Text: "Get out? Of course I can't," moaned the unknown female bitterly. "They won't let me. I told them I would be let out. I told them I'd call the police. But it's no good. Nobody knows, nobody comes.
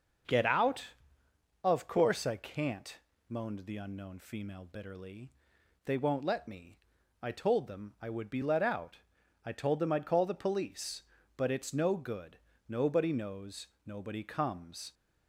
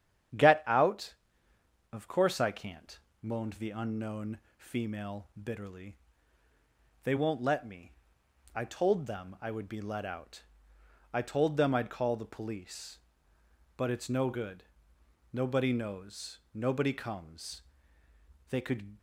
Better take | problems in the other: first | starts louder than the rest; strong; until 2.2 s; 9 dB // pauses between "unknown" and "female"; slight; at 4.3 s; 0.18 s long // goes on to say "They could"; slight; from 18.4 s on; 0.48 s long

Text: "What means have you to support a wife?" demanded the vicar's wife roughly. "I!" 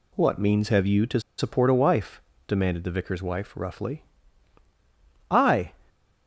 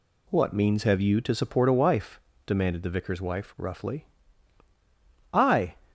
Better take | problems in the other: second | pauses between "to" and "support"; slight; at 1.1 s; 0.18 s long

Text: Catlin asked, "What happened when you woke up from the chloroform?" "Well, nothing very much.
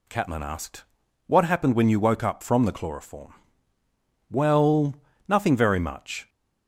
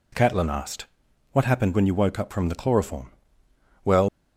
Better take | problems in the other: first | stops before "nothing very much"; at 4.0 s

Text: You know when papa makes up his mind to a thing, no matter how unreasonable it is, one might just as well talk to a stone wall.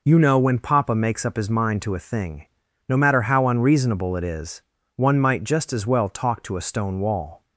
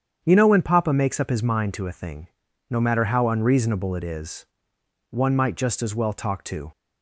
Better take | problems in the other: first | starts louder than the rest; strong; until 1.2 s; 8 dB // stops before "a stone wall"; at 6.7 s

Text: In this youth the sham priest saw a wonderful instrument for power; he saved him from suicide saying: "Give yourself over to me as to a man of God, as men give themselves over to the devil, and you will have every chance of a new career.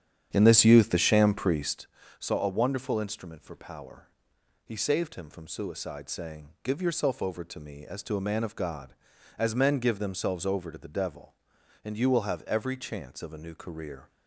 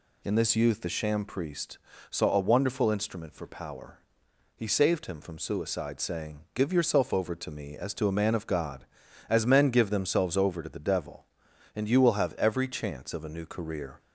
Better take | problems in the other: second | starts louder than the rest; strong; until 1.9 s; 9 dB // pauses between "priest" and "saw"; slight; at 1.8 s; 0.32 s long; slight in the second

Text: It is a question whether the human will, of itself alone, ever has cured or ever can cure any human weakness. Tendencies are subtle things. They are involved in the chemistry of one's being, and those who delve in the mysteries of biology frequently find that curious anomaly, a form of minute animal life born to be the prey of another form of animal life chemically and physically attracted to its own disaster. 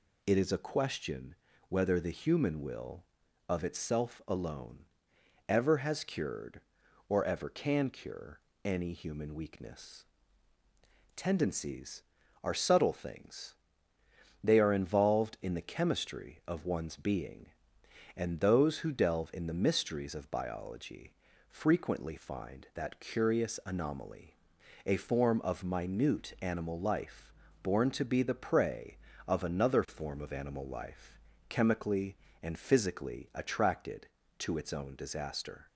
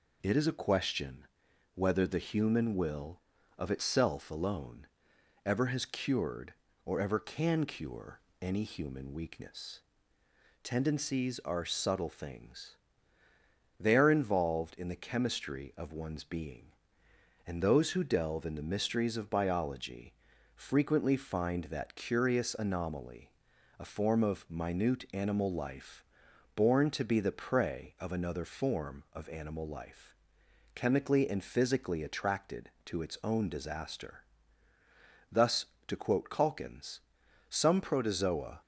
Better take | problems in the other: first | pauses between "question" and "whether"; noticeable; at 1.2 s; 0.48 s long; slight in the first // pauses between "cure" and "any"; slight; at 8.1 s; 0.22 s long; slight in the first // pauses between "biology" and "frequently"; at 20.1 s; 0.42 s long; slight in the first // pauses between "life" and "born"; noticeable; at 26.0 s; 0.52 s long; slight in the first // pauses between "life" and "chemically"; noticeable; at 30.1 s; 0.60 s long; slight in the first // goes on to say "Thus to quote Calkins some protozoa"; strong; from 35.3 s on; 3.3 s long

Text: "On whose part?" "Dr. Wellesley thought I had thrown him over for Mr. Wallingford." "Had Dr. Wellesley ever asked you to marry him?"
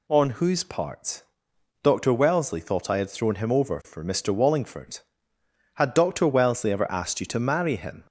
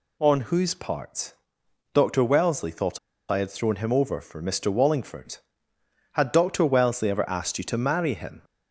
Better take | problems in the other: first | pauses between "thought" and "I"; slight; at 2.9 s; 0.33 s long

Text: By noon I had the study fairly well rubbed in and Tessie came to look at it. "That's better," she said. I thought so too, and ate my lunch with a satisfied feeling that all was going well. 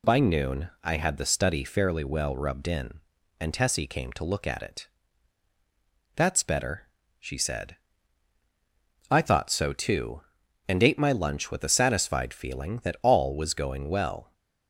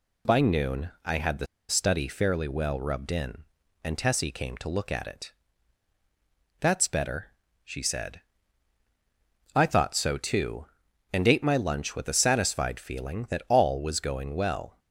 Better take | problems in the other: first | pauses between "the" and "study"; slight; at 1.4 s; 0.22 s long

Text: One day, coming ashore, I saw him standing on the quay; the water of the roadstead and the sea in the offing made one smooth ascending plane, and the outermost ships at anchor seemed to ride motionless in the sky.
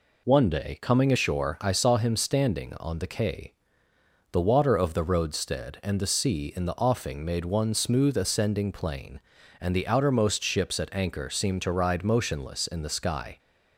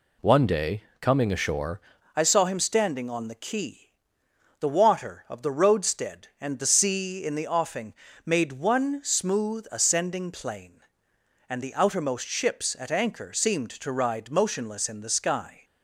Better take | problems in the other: first | changes voice at "I"; from 2.1 s on; 13.5 s long // pauses between "offing" and "made"; slight; at 7.9 s; 0.32 s long

